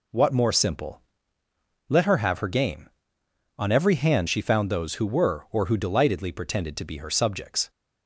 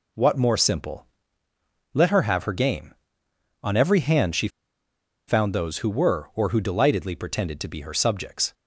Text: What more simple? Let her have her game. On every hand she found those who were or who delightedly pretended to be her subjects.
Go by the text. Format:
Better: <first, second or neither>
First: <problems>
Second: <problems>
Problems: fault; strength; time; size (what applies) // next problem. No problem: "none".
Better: first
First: none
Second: pauses between "she" and "found"; noticeable; at 4.4 s; 0.79 s long